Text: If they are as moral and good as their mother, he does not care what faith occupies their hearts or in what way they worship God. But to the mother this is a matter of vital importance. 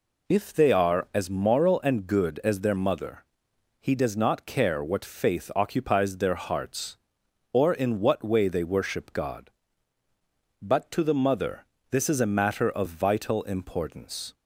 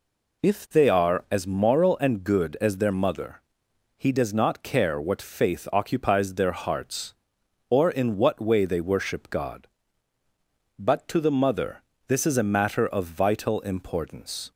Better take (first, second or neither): neither